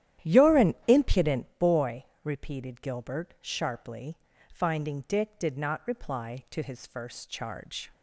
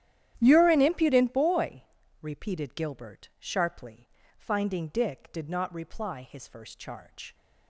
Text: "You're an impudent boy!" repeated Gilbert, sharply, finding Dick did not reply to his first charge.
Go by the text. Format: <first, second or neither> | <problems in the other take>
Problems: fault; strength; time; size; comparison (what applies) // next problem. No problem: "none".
first | starts louder than the rest; strong; until 1.3 s; 11.5 dB; strong in the first // skips "to"; at 6.2 s